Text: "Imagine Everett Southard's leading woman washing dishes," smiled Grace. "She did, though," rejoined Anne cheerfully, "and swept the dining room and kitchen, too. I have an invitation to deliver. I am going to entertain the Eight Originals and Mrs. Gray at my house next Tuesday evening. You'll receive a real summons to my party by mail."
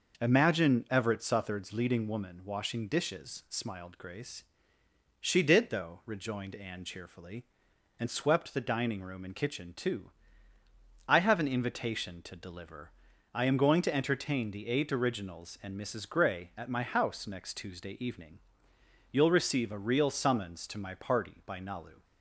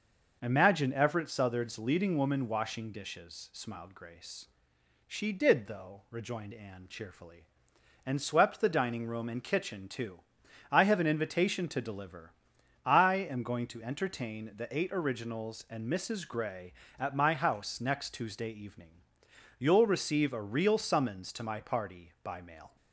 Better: second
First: says "nalu" for "mail"; at 21.5 s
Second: none

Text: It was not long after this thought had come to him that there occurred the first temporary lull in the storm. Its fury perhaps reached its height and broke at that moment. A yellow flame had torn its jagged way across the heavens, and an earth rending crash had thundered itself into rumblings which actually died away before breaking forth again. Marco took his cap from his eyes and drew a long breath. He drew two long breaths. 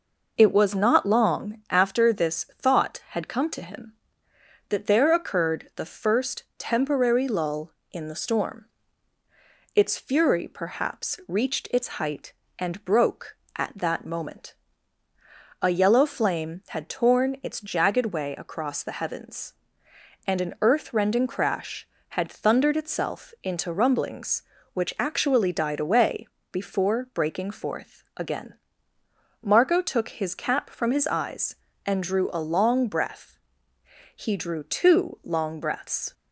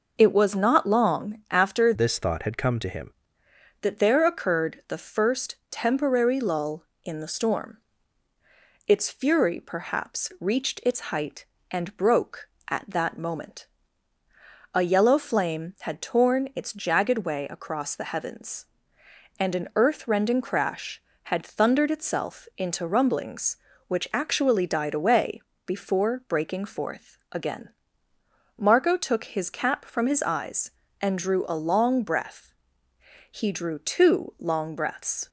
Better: first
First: pauses between "away" and "before"; slight; at 26.2 s; 0.24 s long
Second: changes voice from "this" to "him"; from 1.9 to 3.1 s; 1.2 s long // pauses between "away" and "before"; slight; at 25.4 s; 0.24 s long

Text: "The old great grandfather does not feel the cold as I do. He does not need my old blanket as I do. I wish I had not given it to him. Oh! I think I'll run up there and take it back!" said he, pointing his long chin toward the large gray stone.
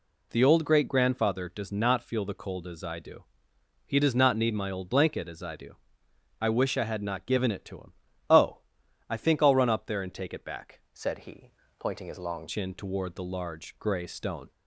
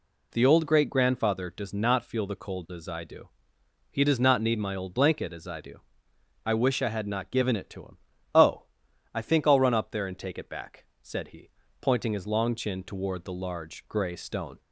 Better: second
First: changes voice from "said" to "long"; from 10.9 to 12.4 s; 1.5 s long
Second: none

